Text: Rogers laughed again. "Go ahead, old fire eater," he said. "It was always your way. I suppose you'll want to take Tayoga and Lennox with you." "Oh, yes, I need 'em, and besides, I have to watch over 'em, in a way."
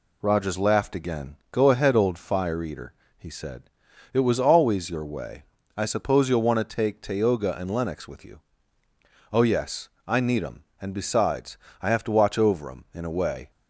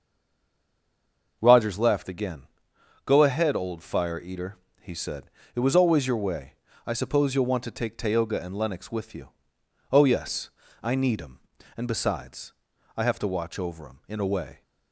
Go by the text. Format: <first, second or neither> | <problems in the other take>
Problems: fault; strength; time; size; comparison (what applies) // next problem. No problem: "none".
first | stays silent before the first word; noticeable; until 1.4 s; 1.4 s long